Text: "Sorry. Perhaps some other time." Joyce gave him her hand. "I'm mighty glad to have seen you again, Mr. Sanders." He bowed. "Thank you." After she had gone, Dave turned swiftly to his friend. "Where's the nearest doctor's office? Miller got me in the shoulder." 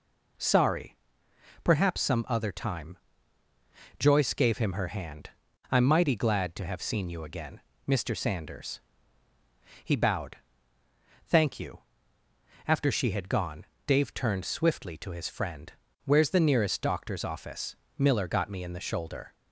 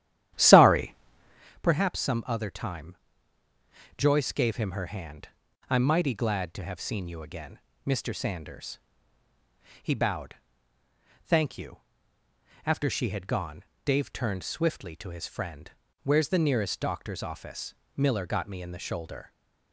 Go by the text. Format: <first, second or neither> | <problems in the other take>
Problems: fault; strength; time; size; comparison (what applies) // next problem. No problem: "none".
first | starts louder than the rest; strong; until 1.5 s; 11.5 dB